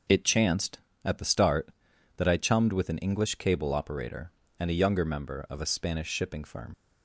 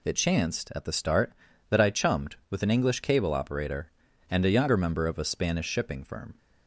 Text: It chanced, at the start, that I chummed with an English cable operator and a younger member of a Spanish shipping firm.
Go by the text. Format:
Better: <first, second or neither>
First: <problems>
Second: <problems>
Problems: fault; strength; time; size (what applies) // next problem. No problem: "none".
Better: second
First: leaves "firm" unfinished; at 6.7 s; 50 ms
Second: none